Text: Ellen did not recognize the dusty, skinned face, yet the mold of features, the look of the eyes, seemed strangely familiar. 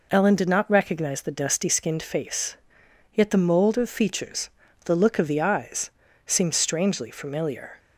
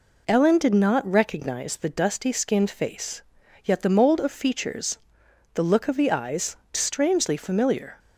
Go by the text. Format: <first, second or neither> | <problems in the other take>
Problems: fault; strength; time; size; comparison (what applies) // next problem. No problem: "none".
first | skips "seemed"; at 6.6 s